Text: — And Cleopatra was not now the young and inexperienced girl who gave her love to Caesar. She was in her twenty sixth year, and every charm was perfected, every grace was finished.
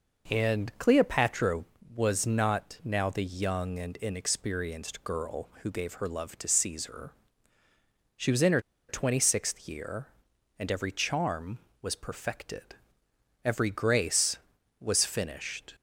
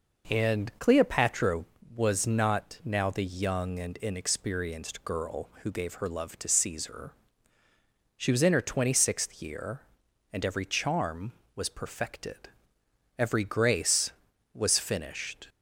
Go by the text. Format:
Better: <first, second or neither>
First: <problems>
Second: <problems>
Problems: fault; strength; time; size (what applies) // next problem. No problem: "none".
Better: second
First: pauses between "her" and "twenty"; slight; at 8.6 s; 0.28 s long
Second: none